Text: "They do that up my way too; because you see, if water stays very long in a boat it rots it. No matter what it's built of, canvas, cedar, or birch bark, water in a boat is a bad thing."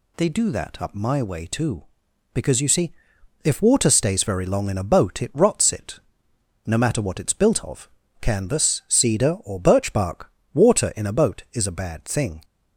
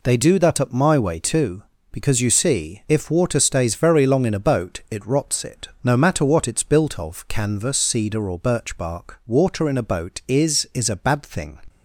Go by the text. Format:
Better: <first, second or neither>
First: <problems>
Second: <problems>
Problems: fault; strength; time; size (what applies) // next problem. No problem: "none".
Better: first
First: none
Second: says "is" twice; at 10.7 s